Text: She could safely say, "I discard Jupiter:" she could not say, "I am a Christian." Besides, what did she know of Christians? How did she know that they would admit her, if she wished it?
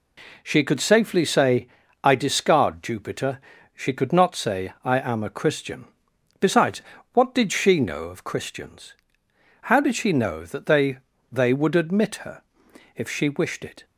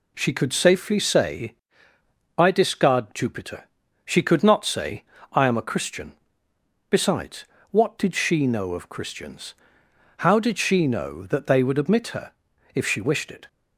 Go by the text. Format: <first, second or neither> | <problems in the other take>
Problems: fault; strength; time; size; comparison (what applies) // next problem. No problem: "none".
second | says "they" twice; at 11.3 s